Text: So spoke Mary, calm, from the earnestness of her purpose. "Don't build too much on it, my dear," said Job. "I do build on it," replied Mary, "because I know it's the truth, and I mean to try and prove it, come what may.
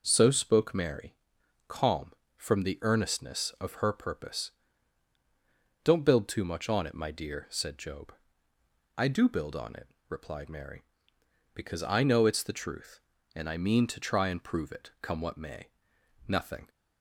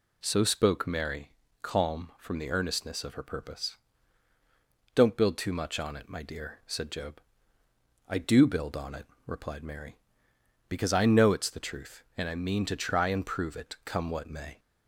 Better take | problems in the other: second | goes on to say "Nothing"; slight; from 16.2 s on; 0.42 s long

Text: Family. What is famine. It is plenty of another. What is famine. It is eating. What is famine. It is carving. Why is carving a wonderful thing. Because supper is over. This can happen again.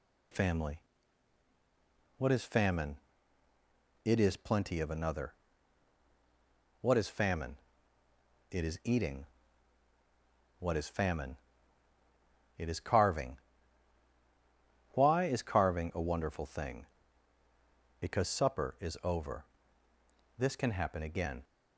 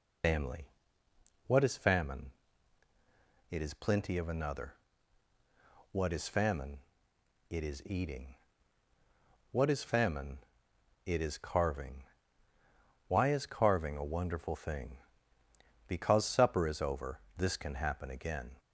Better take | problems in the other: first | loses the start of "Family"; at 0.2 s; 65 ms

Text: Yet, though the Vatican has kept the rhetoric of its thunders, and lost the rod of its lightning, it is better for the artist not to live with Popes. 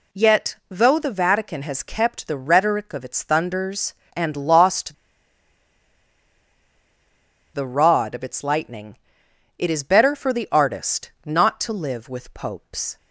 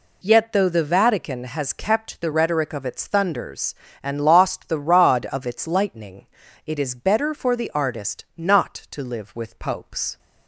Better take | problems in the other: second | pauses between "lost" and "the"; strong; at 4.9 s; 2.6 s long

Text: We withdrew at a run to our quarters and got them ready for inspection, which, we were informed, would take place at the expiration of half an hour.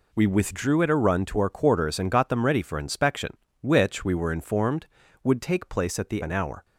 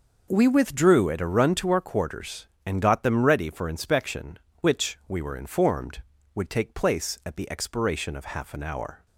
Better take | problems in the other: second | skips "expiration of half"; at 6.2 s

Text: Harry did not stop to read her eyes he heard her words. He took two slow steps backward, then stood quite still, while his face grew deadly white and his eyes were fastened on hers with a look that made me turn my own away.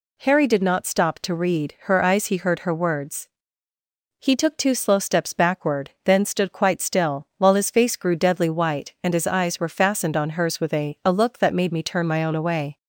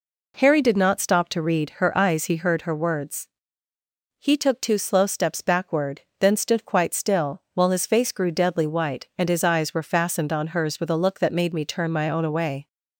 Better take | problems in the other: second | says "a" twice; at 11.0 s

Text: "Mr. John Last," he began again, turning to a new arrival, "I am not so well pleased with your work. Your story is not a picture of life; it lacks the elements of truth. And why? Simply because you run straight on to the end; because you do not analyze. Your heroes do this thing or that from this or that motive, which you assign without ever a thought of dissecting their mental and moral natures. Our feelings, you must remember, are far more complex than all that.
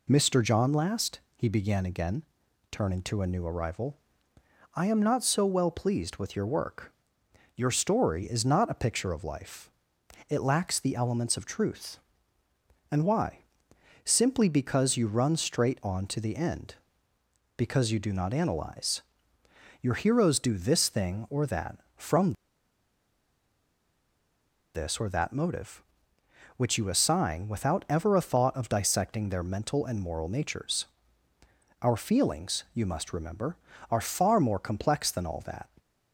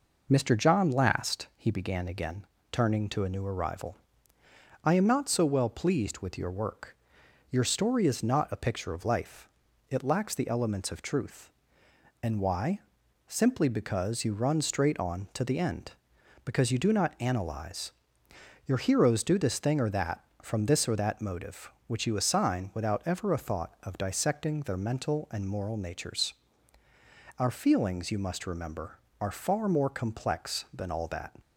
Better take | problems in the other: second | pauses between "from" and "this"; strong; at 22.3 s; 2.4 s long

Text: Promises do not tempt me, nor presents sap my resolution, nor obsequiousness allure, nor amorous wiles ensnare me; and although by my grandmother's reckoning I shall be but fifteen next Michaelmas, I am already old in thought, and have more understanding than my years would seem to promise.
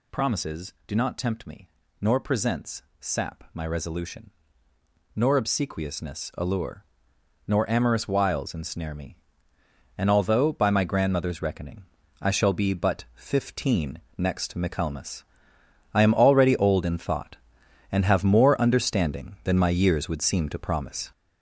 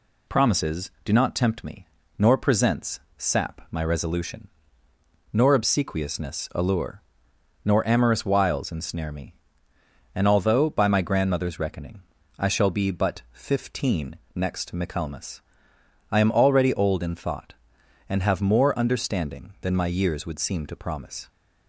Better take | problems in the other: second | gets louder; noticeable; throughout; 6 dB // pauses between "presents" and "sap"; slight; at 2.8 s; 0.18 s long; slight in the second // pauses between "reckoning" and "I"; slight; at 11.8 s; 0.36 s long; slight in the second // pauses between "fifteen" and "next"; slight; at 13.9 s; 0.18 s long; slight in the second

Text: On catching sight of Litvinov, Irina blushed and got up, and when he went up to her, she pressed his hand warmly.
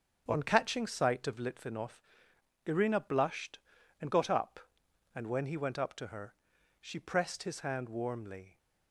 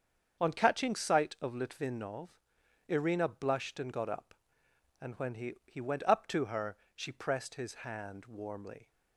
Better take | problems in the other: first | starts louder than the rest; until 1.4 s; 7 dB; strong in the first // says "he" twice; at 5.6 s

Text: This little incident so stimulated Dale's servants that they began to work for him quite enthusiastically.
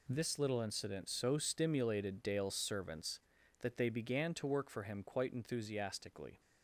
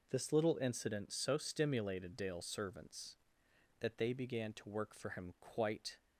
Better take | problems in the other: first | stops before "enthusiastically"; at 5.9 s

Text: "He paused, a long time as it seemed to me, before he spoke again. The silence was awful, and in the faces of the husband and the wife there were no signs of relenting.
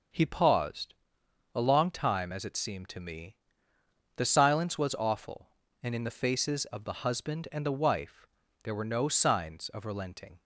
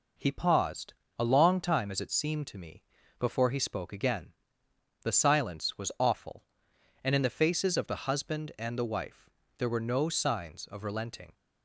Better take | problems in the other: second | skips "before he spoke again"; at 3.7 s // pauses between "wife" and "there"; slight; at 8.2 s; 0.36 s long; slight in the second

